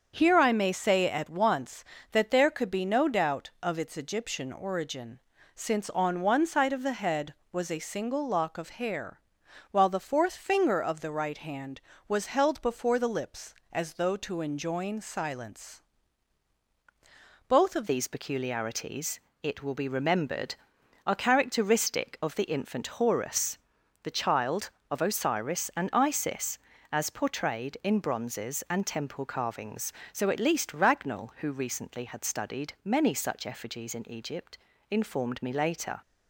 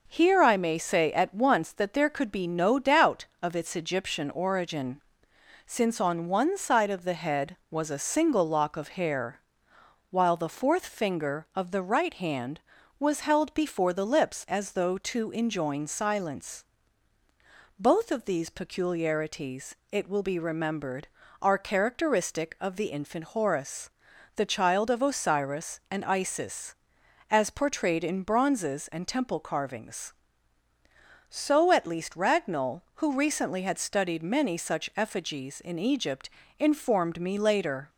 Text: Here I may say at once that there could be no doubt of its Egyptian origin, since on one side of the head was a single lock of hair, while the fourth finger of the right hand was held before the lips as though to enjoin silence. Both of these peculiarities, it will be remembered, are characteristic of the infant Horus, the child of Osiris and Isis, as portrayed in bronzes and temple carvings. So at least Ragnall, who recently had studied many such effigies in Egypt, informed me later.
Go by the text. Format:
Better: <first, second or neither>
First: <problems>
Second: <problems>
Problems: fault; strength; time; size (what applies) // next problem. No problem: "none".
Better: second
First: starts louder than the rest; until 1.1 s; 7 dB // changes voice at "these"; from 17.8 s on; 18.2 s long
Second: none